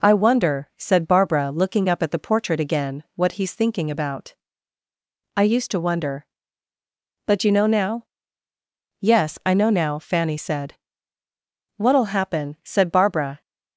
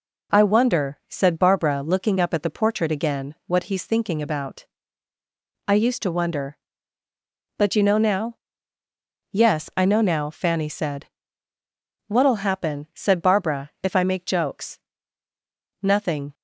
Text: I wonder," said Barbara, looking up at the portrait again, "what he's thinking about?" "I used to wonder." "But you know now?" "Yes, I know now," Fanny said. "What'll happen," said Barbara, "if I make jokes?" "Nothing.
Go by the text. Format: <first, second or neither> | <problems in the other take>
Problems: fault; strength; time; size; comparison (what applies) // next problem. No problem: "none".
second | stops before "if I make jokes Nothing"; at 13.4 s